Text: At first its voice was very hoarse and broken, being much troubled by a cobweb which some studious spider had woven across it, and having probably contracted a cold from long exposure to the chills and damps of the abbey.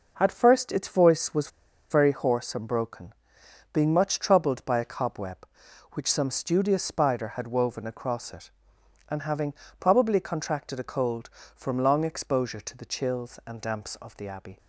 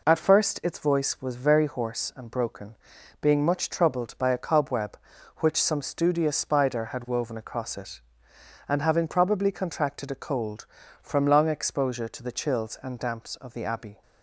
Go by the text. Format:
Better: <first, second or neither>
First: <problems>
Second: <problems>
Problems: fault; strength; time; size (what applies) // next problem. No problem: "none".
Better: second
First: pauses between "was" and "very"; at 1.5 s; 0.41 s long // pauses between "having" and "probably"; slight; at 9.5 s; 0.28 s long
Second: none